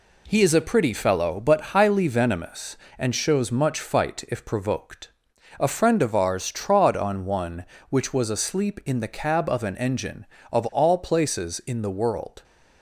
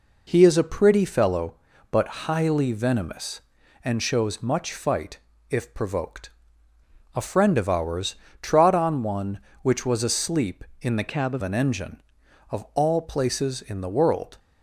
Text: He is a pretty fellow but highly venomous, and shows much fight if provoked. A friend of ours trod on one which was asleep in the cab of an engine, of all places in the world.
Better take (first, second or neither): first